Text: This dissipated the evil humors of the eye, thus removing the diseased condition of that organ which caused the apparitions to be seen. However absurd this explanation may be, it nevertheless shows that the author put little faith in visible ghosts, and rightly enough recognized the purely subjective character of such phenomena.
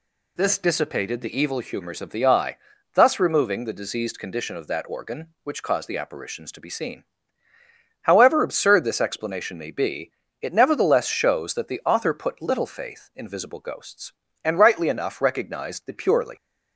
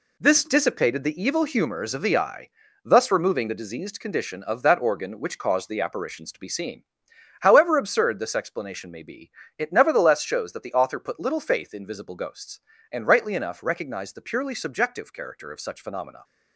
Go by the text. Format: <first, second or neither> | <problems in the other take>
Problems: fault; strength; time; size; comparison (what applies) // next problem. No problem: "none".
second | stops before "subjective character of such phenomena"; at 16.3 s